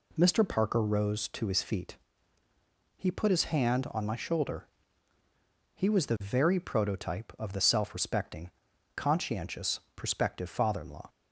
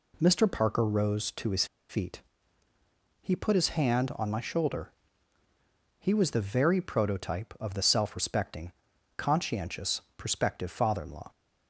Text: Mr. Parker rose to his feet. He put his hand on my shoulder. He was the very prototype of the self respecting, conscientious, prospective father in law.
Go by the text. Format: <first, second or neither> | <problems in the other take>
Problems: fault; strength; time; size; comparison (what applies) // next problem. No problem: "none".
first | pauses between "his" and "feet"; slight; at 1.6 s; 0.24 s long